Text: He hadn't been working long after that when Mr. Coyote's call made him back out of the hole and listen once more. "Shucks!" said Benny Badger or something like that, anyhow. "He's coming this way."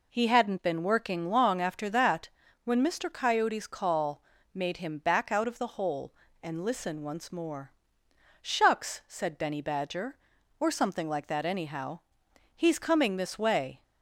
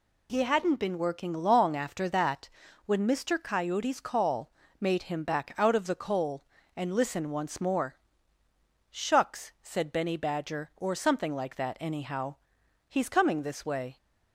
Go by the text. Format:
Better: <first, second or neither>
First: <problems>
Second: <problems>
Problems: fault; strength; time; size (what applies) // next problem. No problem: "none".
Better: first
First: pauses between "that" and "when"; slight; at 2.3 s; 0.34 s long // pauses between "call" and "made"; slight; at 4.2 s; 0.32 s long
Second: pauses between "that" and "when"; at 2.4 s; 0.38 s long // pauses between "call" and "made"; slight; at 4.4 s; 0.30 s long // says "coal" for "hole"; at 5.9 s